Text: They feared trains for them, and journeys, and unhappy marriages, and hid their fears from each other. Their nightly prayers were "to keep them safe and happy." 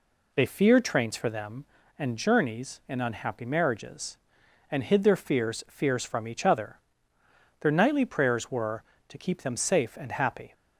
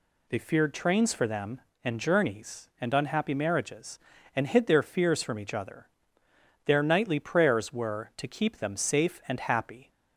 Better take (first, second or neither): second